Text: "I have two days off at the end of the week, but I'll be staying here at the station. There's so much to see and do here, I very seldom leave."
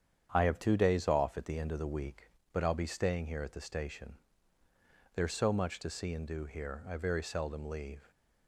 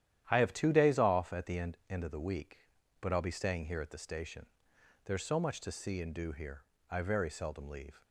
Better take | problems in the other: first | starts louder than the rest; strong; until 1.2 s; 11 dB; strong in the first // says "end" twice; at 1.8 s

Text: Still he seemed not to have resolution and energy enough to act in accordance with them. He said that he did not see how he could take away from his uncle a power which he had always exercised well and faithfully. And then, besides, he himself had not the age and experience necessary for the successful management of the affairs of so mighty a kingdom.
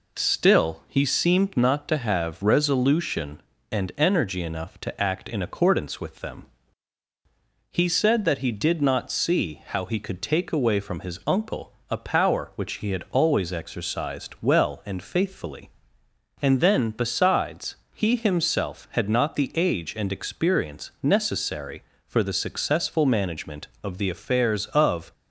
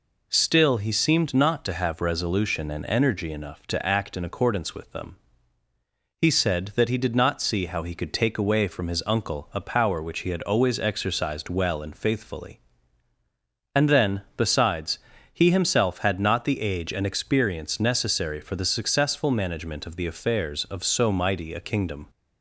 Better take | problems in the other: second | pauses between "uncle" and "a"; slight; at 11.7 s; 0.18 s long // stops before "so mighty a kingdom"; at 25.1 s

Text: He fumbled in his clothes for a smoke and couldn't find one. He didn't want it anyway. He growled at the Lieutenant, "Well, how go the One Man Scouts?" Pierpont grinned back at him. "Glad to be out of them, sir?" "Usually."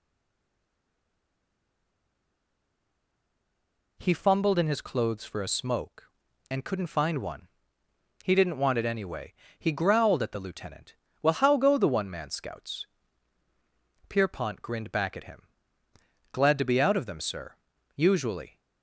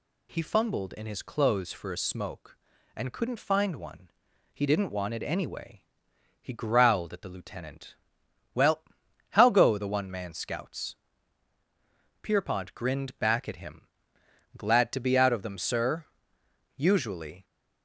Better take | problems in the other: second | stays silent before the first word; strong; until 3.9 s; 3.9 s long

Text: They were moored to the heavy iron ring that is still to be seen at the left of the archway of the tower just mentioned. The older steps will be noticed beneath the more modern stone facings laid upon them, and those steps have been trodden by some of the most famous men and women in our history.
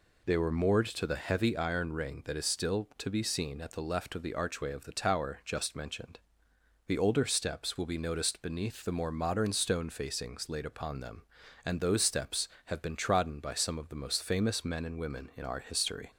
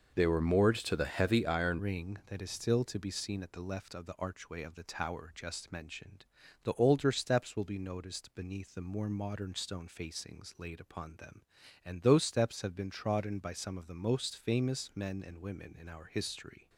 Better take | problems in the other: first | changes voice at "ring"; from 1.7 s on; 14.9 s long

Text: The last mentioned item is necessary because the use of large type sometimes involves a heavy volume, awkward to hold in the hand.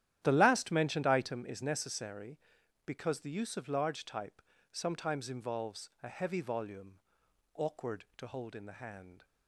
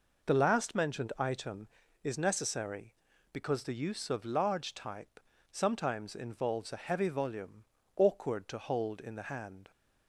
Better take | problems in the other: second | starts louder than the rest; strong; until 1.5 s; 11.5 dB // pauses between "type" and "sometimes"; slight; at 4.4 s; 0.30 s long; slight in the second

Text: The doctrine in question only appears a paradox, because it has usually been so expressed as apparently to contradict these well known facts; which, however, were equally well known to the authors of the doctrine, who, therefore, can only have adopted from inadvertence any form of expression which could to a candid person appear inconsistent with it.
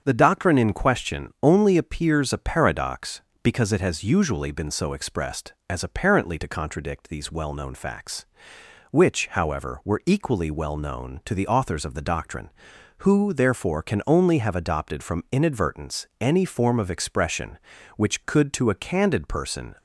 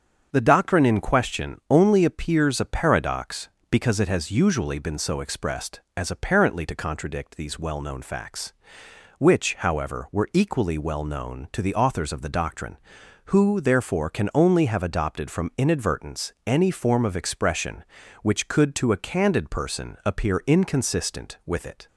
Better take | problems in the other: second | starts louder than the rest; until 1.0 s; 7 dB; also in the second // stops before "appear inconsistent with it"; at 19.7 s

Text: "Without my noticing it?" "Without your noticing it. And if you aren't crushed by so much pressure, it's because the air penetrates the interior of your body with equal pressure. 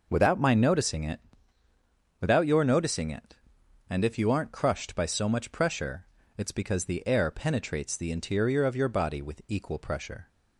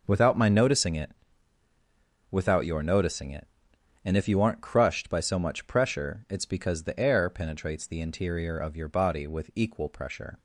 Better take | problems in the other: neither | none

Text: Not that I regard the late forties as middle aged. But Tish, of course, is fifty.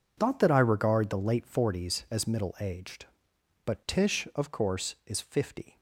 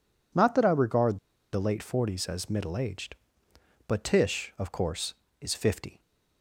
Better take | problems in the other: first | pauses between "regard" and "the"; slight; at 1.1 s; 0.34 s long

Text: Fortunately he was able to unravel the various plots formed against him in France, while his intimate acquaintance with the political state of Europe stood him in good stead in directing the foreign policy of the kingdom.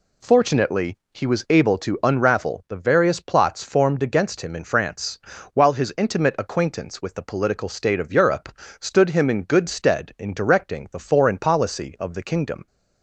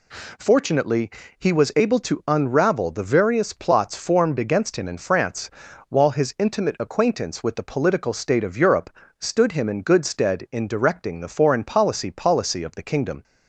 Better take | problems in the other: first | pauses between "Fortunately" and "he"; slight; at 1.0 s; 0.30 s long; slight in the first // pauses between "Europe" and "stood"; slight; at 8.8 s; 0.32 s long; slight in the first // says "policy" twice; at 12.1 s

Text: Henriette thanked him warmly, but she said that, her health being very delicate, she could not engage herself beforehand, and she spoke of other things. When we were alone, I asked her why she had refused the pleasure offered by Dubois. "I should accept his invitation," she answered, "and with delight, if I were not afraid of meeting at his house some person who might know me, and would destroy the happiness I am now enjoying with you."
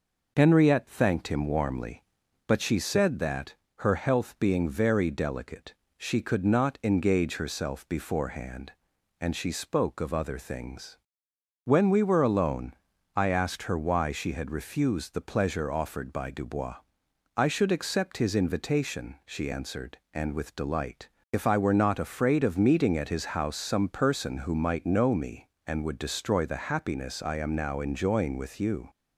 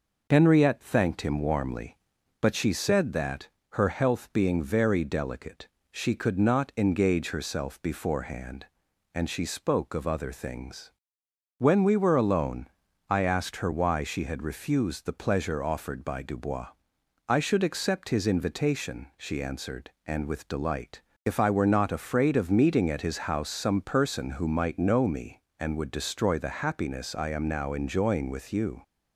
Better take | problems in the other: neither | none

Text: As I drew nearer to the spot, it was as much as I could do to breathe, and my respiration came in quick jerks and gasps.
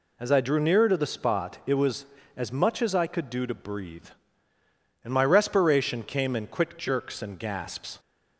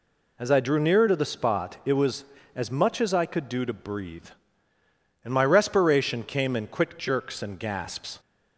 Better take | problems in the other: neither | none

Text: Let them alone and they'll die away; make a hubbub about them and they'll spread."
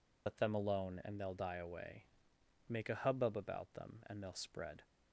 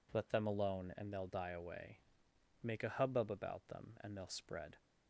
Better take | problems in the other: second | loses the start of "Let"; at 0.2 s; 95 ms

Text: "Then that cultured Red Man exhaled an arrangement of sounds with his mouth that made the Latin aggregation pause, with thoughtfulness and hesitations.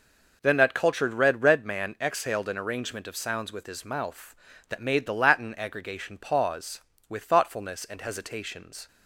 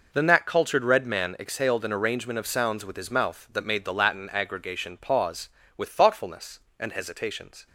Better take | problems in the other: second | says "Red" twice; at 1.4 s

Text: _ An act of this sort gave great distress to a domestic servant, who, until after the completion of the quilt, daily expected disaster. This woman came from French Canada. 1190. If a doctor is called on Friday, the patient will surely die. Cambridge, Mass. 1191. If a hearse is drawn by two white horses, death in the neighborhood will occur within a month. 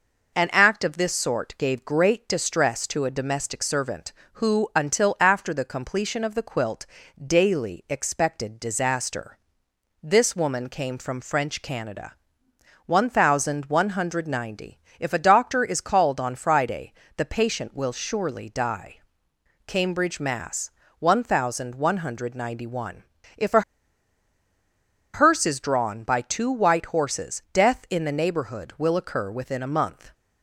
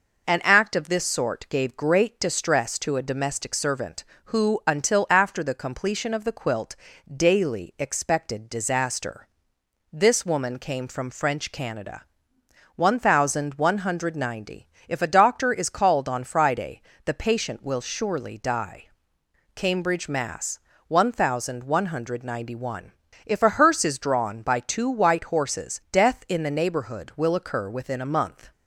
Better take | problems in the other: second | pauses between "a" and "hearse"; strong; at 23.6 s; 1.5 s long

